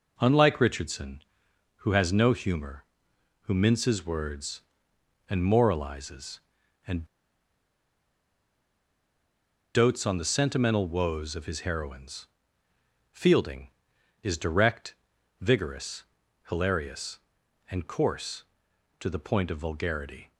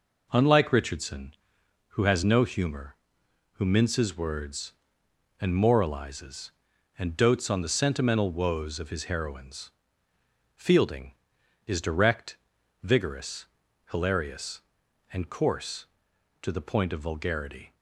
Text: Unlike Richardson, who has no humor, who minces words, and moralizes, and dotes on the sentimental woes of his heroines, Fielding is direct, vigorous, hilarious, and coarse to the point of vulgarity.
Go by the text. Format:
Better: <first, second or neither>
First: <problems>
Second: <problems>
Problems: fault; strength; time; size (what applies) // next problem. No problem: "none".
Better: second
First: pauses between "and" and "dotes"; strong; at 7.0 s; 2.7 s long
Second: none